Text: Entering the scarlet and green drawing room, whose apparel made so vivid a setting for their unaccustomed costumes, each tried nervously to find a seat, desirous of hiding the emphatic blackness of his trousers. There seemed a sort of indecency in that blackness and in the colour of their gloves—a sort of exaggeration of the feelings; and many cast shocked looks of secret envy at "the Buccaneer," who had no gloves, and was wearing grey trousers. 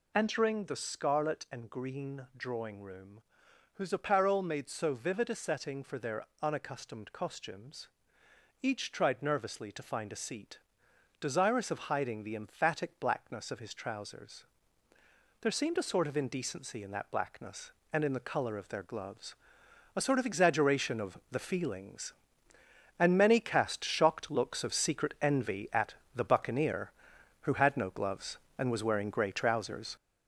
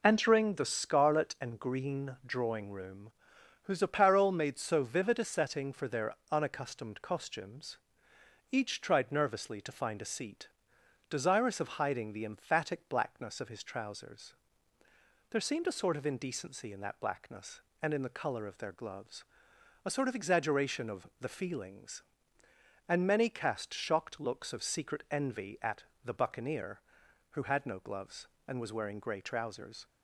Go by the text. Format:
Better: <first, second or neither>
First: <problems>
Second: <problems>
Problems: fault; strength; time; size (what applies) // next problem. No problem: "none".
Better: second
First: gets louder; noticeable; throughout; 5.5 dB // pauses between "their" and "unaccustomed"; slight; at 6.2 s; 0.16 s long // pauses between "at" and "the"; slight; at 25.9 s; 0.22 s long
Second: pauses between "their" and "unaccustomed"; slight; at 6.1 s; 0.16 s long // pauses between "at" and "the"; slight; at 25.8 s; 0.22 s long